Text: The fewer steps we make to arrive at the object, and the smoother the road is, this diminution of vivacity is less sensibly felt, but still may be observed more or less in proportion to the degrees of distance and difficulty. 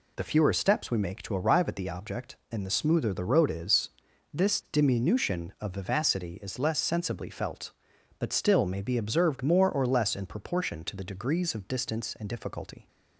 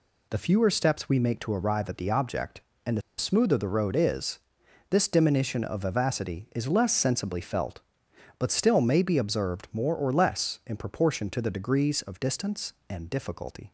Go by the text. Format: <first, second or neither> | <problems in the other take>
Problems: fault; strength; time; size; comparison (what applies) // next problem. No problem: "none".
first | pauses between "the" and "smoother"; slight; at 3.0 s; 0.17 s long